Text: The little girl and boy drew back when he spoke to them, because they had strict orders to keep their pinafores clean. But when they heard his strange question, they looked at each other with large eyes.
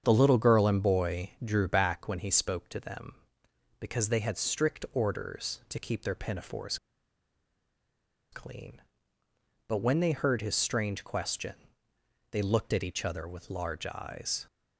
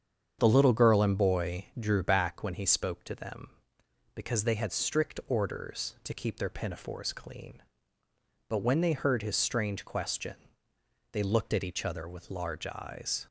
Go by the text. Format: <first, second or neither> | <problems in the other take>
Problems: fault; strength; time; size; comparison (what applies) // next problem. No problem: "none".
second | starts louder than the rest; strong; until 1.0 s; 7.5 dB; strong in the second // pauses between "pinafores" and "clean"; strong; at 6.7 s; 1.5 s long